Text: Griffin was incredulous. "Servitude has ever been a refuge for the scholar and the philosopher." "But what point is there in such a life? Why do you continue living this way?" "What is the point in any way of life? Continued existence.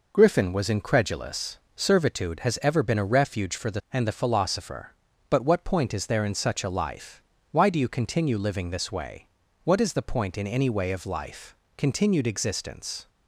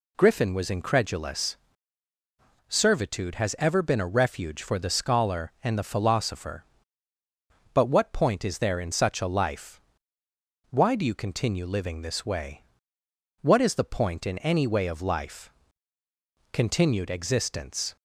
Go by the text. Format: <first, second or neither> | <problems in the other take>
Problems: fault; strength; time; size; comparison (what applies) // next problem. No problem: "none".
second | skips "scholar"; at 3.8 s